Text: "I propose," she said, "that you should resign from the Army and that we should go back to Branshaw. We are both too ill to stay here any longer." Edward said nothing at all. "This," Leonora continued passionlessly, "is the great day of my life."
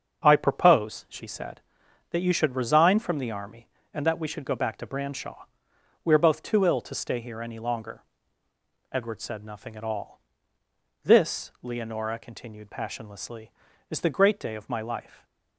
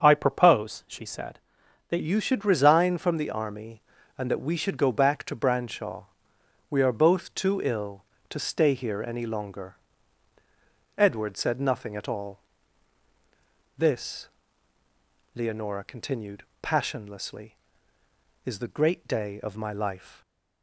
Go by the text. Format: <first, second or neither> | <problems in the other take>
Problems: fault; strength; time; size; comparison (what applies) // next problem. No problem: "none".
first | starts louder than the rest; until 1.0 s; 6.5 dB; also in the first // changes voice at "you"; from 2.0 s on; 18.2 s long // pauses between "continued" and "passionlessly"; slight; at 16.4 s; 0.18 s long